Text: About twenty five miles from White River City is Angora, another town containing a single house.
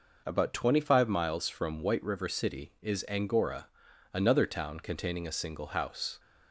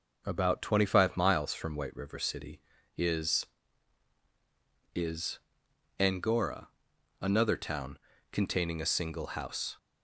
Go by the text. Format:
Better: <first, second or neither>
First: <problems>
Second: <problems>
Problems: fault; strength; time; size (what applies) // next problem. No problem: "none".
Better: first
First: none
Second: says "is" twice; at 4.9 s // pauses between "town" and "containing"; slight; at 7.9 s; 0.34 s long